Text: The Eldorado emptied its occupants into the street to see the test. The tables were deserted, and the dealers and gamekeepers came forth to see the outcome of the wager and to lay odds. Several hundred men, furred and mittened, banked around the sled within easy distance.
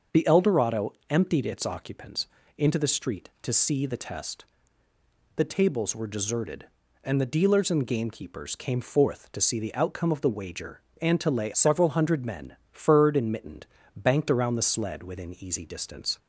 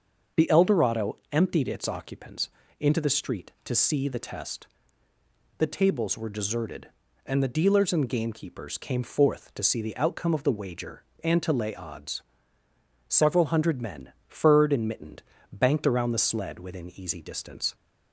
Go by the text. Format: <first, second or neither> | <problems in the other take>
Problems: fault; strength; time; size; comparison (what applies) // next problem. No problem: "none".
second | starts louder than the rest; until 1.2 s; 6.5 dB; also in the second // pauses between "Eldorado" and "emptied"; slight; at 0.9 s; 0.16 s long // pauses between "occupants" and "into"; slight; at 2.2 s; 0.30 s long; slight in the second // skips "odds"; at 11.5 s